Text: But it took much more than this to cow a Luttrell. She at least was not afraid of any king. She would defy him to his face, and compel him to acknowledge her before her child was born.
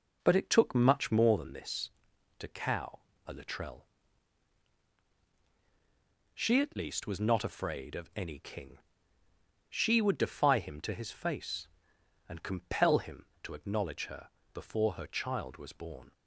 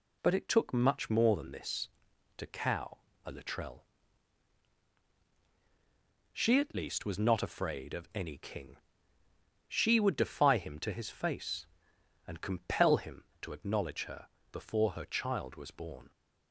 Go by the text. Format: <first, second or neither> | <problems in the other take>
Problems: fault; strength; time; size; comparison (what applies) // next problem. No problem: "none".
second | starts louder than the rest; noticeable; until 1.4 s; 4.5 dB // pauses between "cow" and "a"; slight; at 3.0 s; 0.26 s long; slight in the second // pauses between "her" and "before"; slight; at 14.2 s; 0.26 s long; slight in the second